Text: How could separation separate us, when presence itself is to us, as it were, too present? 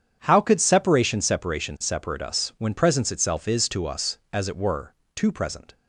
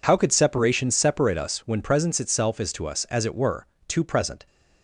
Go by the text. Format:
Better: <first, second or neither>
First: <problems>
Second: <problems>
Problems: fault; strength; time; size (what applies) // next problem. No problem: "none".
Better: second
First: starts louder than the rest; strong; until 1.2 s; 8.5 dB // says "separation" twice; at 1.2 s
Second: none